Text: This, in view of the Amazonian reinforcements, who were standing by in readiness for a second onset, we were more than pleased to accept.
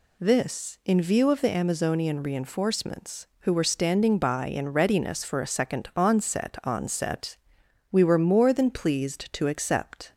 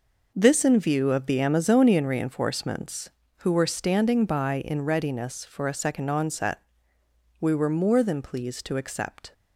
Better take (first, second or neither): second